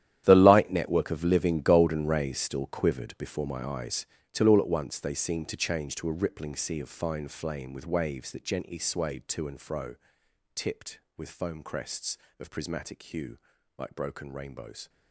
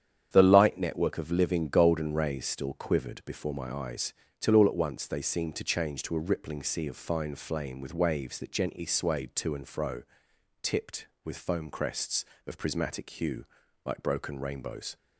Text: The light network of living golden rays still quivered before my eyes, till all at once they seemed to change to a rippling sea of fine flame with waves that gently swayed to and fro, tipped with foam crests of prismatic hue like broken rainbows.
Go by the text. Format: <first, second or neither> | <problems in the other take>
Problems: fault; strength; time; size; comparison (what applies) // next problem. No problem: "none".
second | gets quieter; strong; throughout; 14.5 dB // starts louder than the rest; strong; until 1.2 s; 11 dB; strong in the second // pauses between "hue" and "like"; at 13.3 s; 0.40 s long; also in the second